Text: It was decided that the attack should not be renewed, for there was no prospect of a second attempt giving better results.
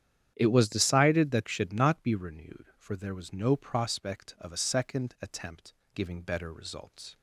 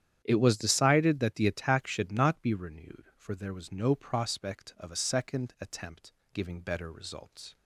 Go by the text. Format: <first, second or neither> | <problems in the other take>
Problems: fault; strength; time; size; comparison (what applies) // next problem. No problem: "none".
second | starts louder than the rest; strong; until 1.3 s; 10 dB; strong in the second // skips "the attack"; at 1.4 s // pauses between "attempt" and "giving"; slight; at 5.7 s; 0.18 s long; slight in the second